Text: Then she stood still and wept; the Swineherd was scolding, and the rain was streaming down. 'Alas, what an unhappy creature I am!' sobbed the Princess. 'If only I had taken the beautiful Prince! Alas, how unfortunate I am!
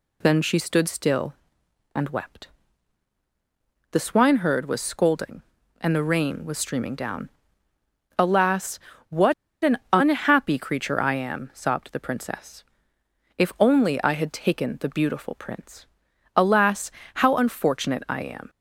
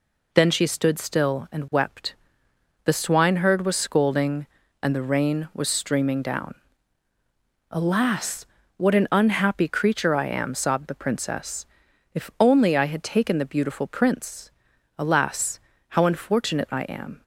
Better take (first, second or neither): second